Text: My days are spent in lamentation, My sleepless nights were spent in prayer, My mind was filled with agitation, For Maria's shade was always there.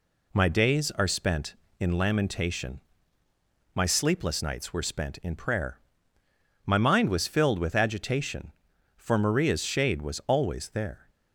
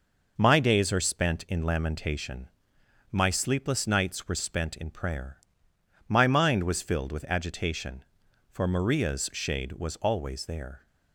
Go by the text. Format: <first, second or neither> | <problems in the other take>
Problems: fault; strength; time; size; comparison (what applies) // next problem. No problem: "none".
neither | none